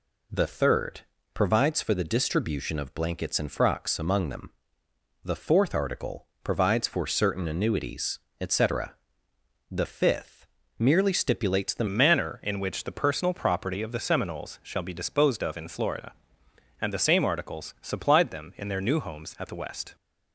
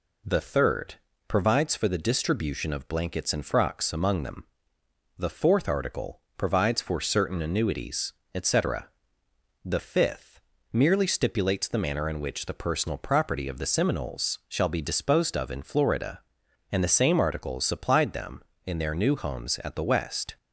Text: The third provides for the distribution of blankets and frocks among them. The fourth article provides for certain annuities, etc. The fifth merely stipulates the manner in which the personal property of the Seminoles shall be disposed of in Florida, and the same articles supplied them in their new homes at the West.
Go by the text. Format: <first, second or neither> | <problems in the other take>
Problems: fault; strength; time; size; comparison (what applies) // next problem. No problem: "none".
second | pauses between "third" and "provides"; slight; at 1.0 s; 0.34 s long; slight in the second // pauses between "article" and "provides"; slight; at 6.2 s; 0.18 s long; slight in the second // pauses between "fifth" and "merely"; slight; at 10.4 s; 0.32 s long; slight in the second // changes voice at "manner"; from 11.8 s on; 8.1 s long